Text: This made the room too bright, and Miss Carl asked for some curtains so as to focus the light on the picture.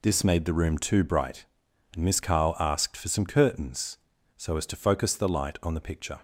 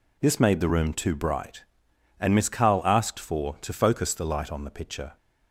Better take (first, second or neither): first